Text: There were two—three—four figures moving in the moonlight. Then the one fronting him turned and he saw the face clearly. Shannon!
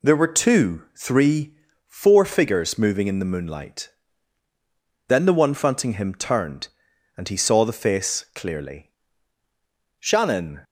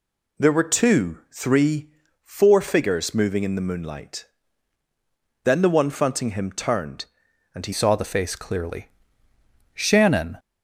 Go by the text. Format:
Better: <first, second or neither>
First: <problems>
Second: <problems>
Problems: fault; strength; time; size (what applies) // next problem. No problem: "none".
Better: first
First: none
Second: changes voice at "saw"; from 7.7 s on; 2.6 s long